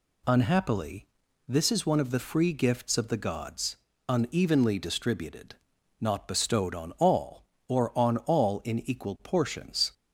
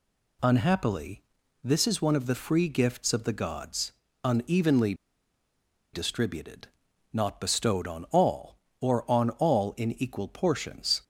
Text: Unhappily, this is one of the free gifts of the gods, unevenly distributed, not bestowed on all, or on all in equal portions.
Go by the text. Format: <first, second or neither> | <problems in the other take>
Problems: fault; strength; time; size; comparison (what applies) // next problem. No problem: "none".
first | pauses between "unevenly" and "distributed"; at 4.9 s; 0.99 s long